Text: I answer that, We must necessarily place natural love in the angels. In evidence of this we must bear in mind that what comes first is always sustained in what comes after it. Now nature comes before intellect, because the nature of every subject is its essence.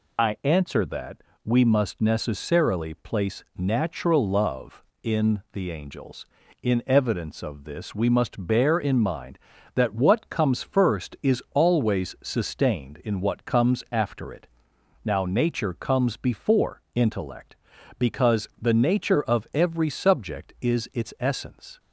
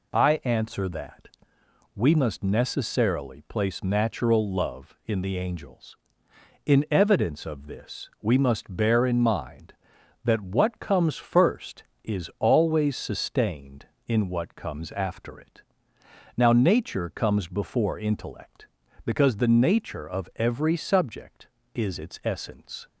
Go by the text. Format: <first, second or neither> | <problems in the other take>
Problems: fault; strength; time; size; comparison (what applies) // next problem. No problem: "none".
second | loses the start of "I"; at 0.1 s; 35 ms